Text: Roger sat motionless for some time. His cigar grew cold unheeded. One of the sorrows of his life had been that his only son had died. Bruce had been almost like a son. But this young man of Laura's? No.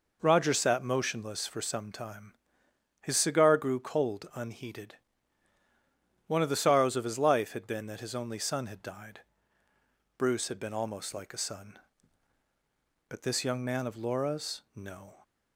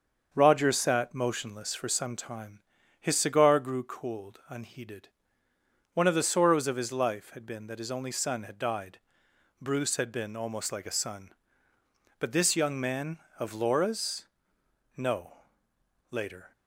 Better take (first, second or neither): first